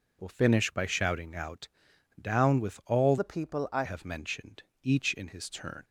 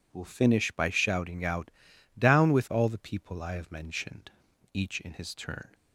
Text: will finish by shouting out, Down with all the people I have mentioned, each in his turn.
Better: second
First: changes voice from "the" to "I"; from 3.1 to 3.8 s; 0.7 s long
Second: none

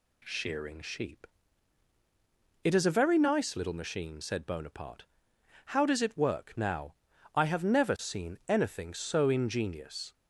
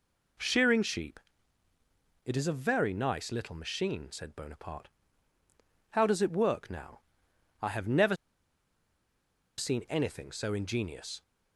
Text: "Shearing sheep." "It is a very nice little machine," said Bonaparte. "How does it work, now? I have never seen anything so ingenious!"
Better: first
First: none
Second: pauses between "never" and "seen"; strong; at 8.1 s; 1.4 s long

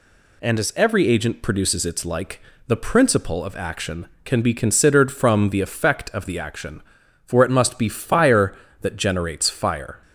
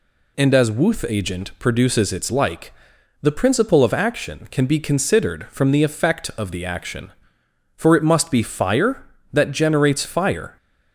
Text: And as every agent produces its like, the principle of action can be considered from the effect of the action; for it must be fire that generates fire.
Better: first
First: none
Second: says "wuth" for "every"; at 0.7 s

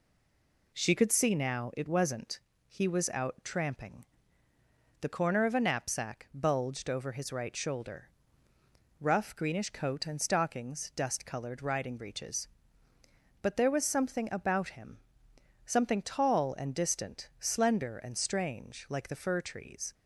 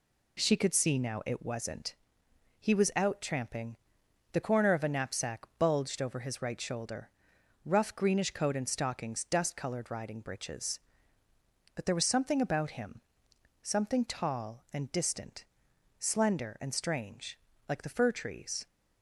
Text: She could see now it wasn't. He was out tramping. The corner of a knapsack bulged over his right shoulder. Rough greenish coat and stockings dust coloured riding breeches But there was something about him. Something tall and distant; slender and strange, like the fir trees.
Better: second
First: stays silent before the first word; slight; until 0.7 s; 0.7 s long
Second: none

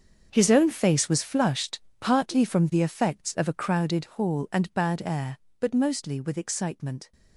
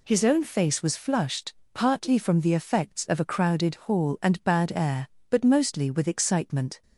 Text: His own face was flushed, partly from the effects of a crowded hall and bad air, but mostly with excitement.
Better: second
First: gets quieter; strong; throughout; 13.5 dB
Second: none

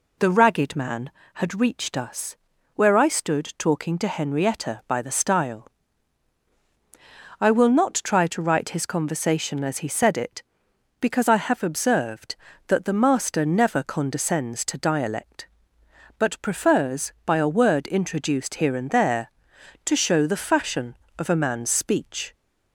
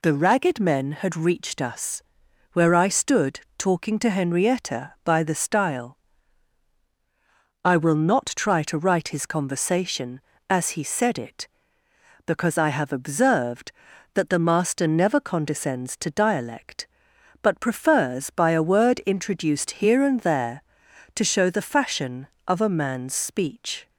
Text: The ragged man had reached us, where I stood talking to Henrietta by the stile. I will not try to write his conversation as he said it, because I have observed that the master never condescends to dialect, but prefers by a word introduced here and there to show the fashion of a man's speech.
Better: first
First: none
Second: says "men" for "man"; at 0.5 s // pauses between "stood" and "talking"; slight; at 3.4 s; 0.18 s long

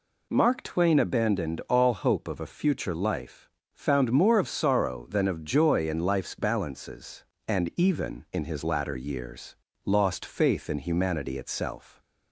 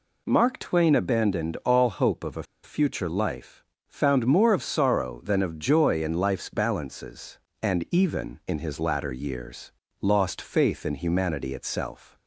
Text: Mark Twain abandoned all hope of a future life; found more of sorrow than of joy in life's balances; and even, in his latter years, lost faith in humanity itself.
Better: first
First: none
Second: pauses between "a" and "future"; slight; at 2.4 s; 0.19 s long

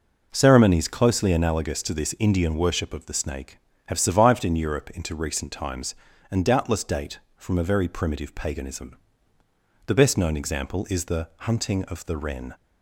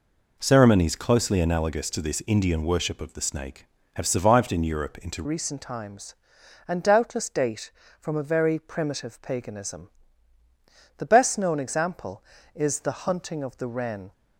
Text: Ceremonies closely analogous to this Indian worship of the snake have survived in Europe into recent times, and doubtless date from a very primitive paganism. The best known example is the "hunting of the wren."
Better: first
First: none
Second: changes voice at "recent"; from 5.2 s on; 8.9 s long

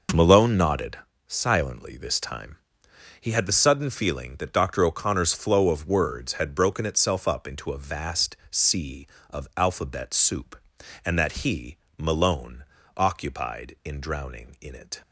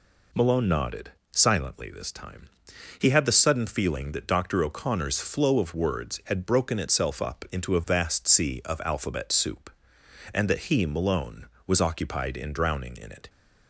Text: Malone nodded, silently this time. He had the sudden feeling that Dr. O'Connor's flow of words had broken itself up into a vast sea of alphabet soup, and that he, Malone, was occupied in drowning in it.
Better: second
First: skips "was"; at 12.8 s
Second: none

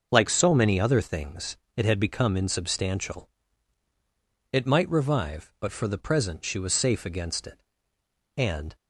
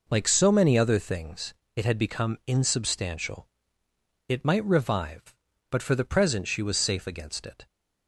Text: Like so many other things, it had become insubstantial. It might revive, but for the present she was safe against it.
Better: second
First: starts louder than the rest; noticeable; until 1.1 s; 6 dB // goes on to say "And"; slight; from 8.3 s on; 0.40 s long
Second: none

